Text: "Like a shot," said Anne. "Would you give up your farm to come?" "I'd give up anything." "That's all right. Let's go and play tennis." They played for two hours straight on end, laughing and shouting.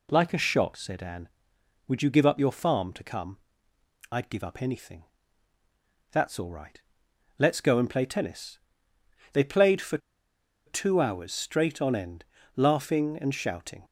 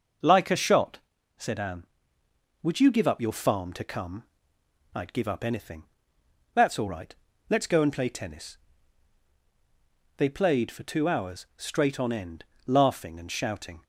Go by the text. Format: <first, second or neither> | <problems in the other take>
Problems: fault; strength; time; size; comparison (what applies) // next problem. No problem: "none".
second | pauses between "for" and "two"; noticeable; at 9.9 s; 0.68 s long